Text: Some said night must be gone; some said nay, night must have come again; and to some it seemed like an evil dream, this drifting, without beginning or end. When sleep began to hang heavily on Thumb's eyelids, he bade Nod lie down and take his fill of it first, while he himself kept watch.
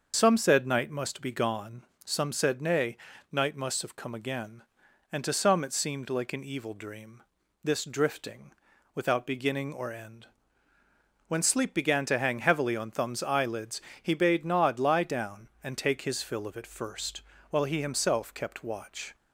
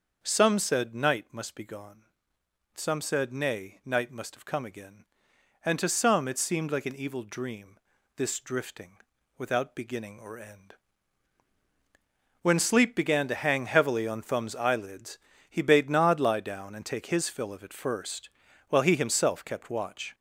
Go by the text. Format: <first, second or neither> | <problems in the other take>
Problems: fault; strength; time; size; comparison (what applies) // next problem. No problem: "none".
first | gets louder; noticeable; throughout; 4 dB // starts louder than the rest; until 1.2 s; 6.5 dB; also in the first